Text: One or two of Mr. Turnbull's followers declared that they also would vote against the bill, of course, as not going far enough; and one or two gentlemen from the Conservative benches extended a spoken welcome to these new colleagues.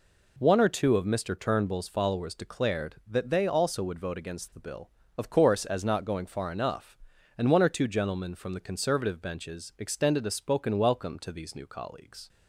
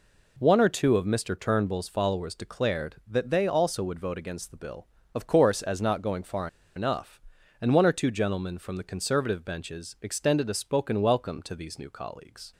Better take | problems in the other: first | pauses between "far" and "enough"; slight; at 6.4 s; 0.28 s long

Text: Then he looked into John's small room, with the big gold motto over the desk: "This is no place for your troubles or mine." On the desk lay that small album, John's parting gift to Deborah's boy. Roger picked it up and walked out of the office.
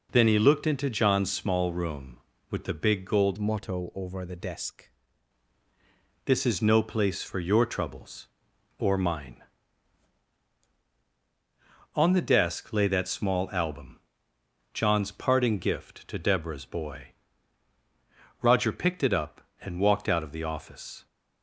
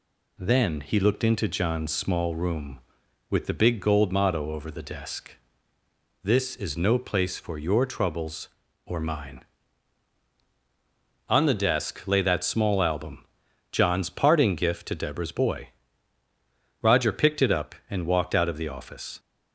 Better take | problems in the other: second | changes voice from "motto" to "desk"; from 3.3 to 4.8 s; 1.5 s long

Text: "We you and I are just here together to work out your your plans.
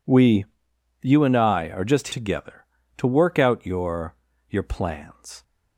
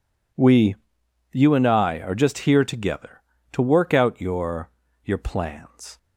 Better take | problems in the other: second | pauses between "We" and "you"; noticeable; at 0.4 s; 0.56 s long; noticeable in the second // skips "here"; at 2.0 s // pauses between "your" and "your"; slight; at 4.1 s; 0.34 s long; slight in the second

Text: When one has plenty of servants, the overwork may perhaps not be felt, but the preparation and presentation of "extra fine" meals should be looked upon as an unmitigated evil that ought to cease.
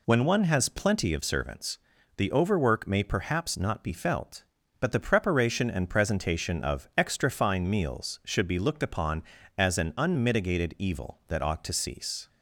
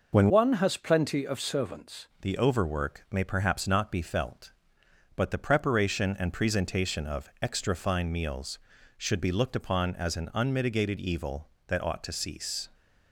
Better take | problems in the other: first | changes voice from "one" to "servants"; from 0.2 to 2.0 s; 1.8 s long

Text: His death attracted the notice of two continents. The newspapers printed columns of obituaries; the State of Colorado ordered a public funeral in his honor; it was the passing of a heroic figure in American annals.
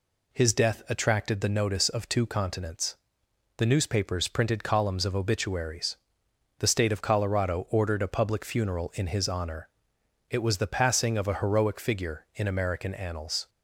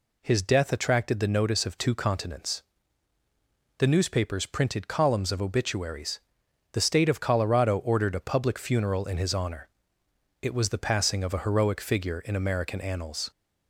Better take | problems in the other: neither | none

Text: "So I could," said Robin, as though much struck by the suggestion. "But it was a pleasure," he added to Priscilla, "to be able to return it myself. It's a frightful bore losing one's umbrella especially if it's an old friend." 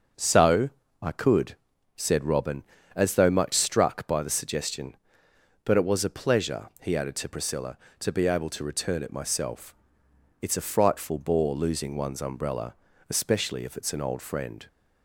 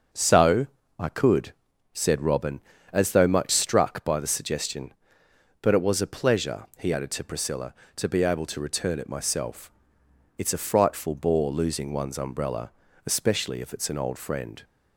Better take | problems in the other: neither | starts louder than the rest; noticeable; the same in both // pauses between "So" and "I"; slight; the same in both // pauses between "umbrella" and "especially"; slight; the same in both

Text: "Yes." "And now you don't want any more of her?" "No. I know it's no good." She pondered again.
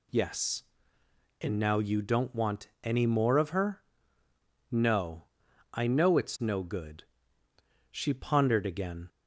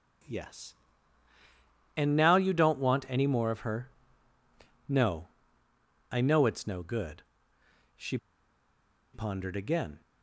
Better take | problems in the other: first | pauses between "She" and "pondered"; noticeable; at 8.1 s; 0.97 s long

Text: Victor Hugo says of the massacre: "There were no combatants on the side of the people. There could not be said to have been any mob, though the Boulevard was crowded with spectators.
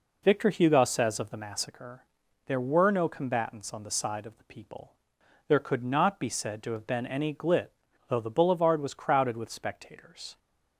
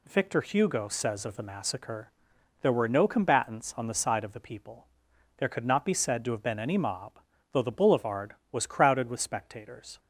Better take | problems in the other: second | says "glit" for "mob"; at 7.3 s

